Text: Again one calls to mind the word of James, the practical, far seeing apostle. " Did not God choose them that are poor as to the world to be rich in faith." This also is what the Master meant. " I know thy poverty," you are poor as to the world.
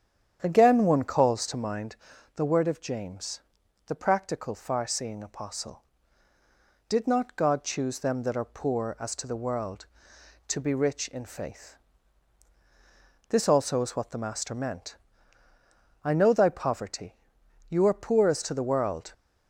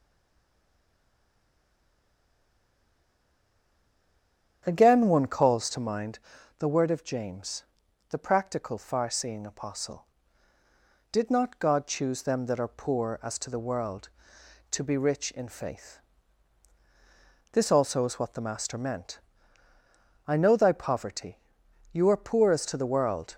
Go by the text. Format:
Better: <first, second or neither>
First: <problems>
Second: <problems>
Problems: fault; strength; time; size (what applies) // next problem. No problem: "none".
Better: first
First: starts louder than the rest; strong; until 1.4 s; 9.5 dB // pauses between "mind" and "the"; at 1.9 s; 0.38 s long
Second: stays silent before the first word; strong; until 4.6 s; 4.6 s long // starts louder than the rest; strong; until 5.6 s; 9.5 dB // pauses between "mind" and "the"; at 6.1 s; 0.38 s long